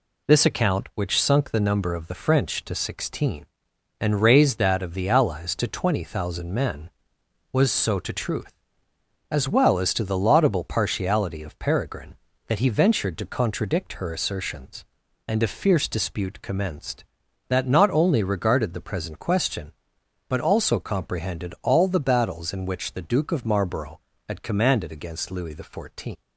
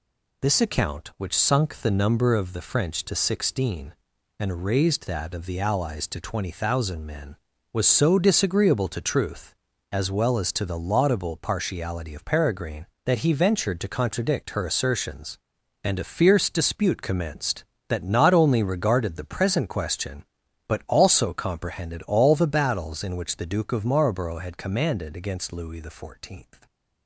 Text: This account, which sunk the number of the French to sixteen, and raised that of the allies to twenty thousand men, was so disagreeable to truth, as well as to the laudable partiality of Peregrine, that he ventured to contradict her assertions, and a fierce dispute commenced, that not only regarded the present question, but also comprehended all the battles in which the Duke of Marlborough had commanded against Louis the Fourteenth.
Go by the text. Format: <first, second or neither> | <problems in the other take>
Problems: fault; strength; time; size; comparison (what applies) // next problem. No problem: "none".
second | skips "disagreeable"; at 7.9 s